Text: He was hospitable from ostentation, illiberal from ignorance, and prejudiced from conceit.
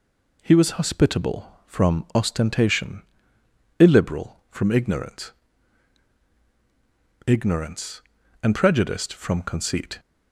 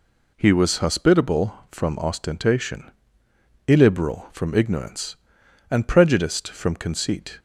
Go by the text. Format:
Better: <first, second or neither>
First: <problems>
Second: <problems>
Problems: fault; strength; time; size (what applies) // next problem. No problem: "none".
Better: second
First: says "ignorance" twice; at 7.2 s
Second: none